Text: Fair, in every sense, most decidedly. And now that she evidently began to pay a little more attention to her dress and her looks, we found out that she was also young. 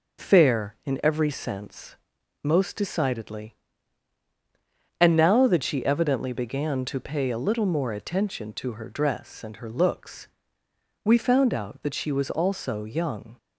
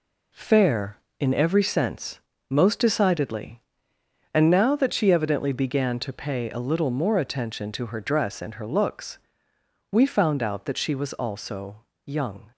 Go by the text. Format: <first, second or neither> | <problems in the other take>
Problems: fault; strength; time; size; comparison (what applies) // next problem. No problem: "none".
first | gets quieter; throughout; 7 dB // pauses between "also" and "young"; slight; at 11.7 s; 0.26 s long